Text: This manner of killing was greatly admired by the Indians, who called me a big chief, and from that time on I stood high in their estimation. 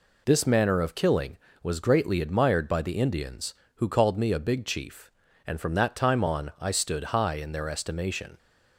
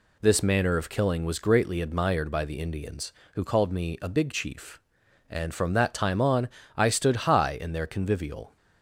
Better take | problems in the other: first | pauses between "on" and "I"; slight; at 6.4 s; 0.28 s long // says "convivial" for "estimation"; at 7.8 s

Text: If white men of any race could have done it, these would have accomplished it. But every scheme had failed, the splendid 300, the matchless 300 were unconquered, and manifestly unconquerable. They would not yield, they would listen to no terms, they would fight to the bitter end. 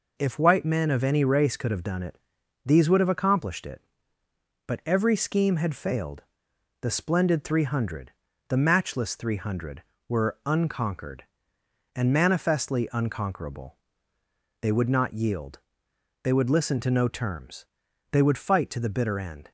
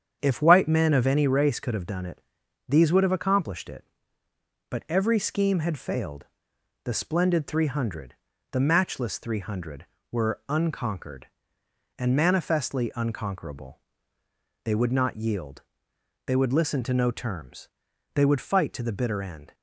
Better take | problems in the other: first | starts louder than the rest; strong; until 1.3 s; 8 dB

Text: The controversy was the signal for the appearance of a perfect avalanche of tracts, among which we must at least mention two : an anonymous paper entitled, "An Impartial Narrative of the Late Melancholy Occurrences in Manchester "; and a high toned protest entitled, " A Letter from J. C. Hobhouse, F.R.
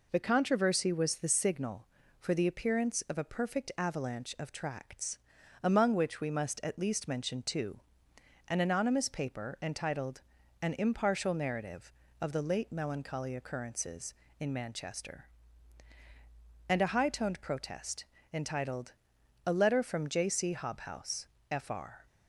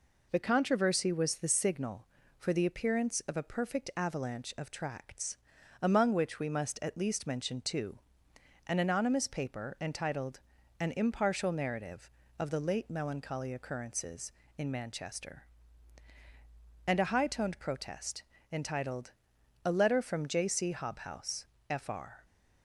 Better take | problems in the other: neither | pauses between "protest" and "entitled"; slight; the same in both

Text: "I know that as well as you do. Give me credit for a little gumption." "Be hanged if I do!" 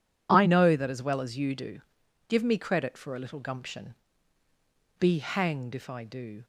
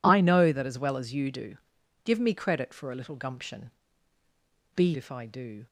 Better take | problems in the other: first | skips "hanged"; at 4.9 s

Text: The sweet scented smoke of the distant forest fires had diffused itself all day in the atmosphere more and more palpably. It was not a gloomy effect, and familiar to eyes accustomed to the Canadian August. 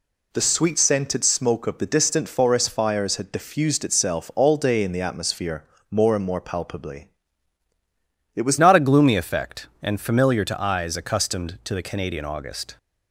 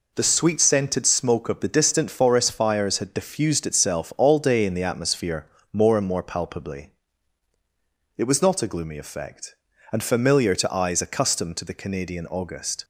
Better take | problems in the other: second | pauses between "atmosphere" and "more"; slight; at 5.6 s; 0.26 s long; slight in the second // changes voice at "not"; from 8.5 s on; 4.2 s long

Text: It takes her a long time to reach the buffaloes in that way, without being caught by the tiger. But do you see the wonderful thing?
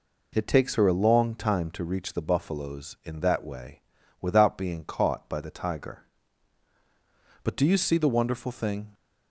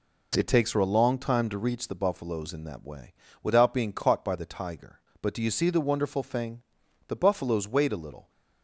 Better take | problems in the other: first | goes on to say "The buffaloes wait a little"; noticeable; from 7.0 s on; 1.2 s long

